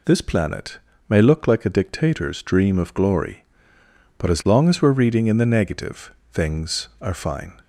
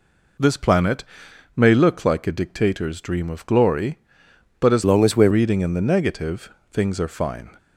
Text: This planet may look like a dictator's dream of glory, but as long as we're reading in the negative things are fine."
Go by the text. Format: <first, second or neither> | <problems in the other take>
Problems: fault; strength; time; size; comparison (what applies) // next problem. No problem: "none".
first | pauses between "planet" and "may"; noticeable; at 1.0 s; 0.52 s long; slight in the first // changes voice from "long" to "we're"; from 4.8 to 5.3 s; 0.5 s long // pauses between "negative" and "things"; slight; at 6.5 s; 0.22 s long; slight in the first